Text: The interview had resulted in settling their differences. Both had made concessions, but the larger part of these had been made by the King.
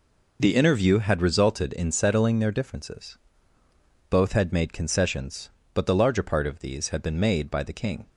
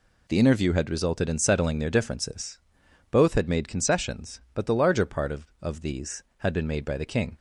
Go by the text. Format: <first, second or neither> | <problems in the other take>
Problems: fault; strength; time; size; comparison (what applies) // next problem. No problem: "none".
first | says "of" twice; at 5.6 s